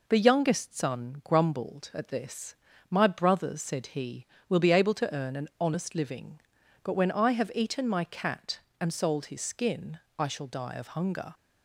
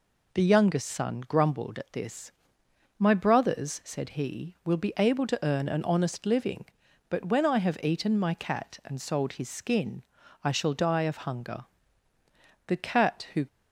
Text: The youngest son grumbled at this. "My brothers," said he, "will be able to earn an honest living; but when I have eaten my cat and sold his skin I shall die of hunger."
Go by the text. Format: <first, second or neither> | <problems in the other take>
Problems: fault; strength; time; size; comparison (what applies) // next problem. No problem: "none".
first | pauses between "skin" and "I"; at 10.0 s; 0.38 s long; slight in the first // goes on to say "The Cat who"; noticeable; from 12.6 s on; 0.80 s long